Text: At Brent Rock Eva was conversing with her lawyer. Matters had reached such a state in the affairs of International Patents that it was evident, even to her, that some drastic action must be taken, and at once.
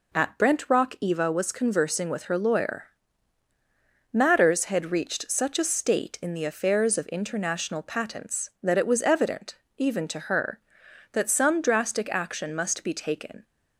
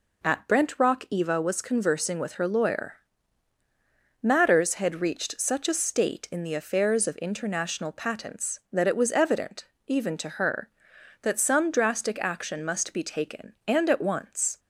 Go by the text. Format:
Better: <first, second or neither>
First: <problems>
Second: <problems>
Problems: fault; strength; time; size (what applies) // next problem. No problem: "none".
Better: second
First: stops before "and at once"; at 13.4 s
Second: none